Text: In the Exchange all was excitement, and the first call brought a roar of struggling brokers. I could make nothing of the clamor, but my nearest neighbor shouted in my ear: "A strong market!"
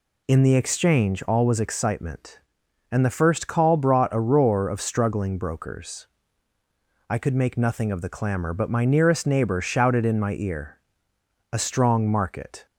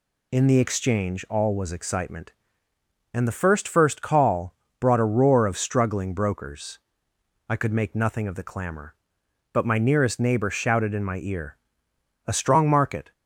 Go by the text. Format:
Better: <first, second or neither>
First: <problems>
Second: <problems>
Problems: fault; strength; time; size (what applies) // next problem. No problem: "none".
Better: first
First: none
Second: says "first" twice; at 3.6 s // pauses between "call" and "brought"; slight; at 4.5 s; 0.26 s long